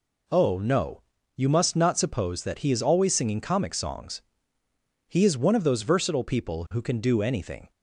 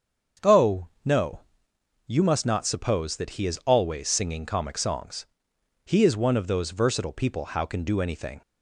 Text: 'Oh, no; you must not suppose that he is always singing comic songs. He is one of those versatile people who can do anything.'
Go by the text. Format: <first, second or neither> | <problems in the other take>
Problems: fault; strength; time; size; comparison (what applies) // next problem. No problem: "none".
first | starts louder than the rest; strong; until 2.2 s; 7 dB // says "how" for "who"; at 7.4 s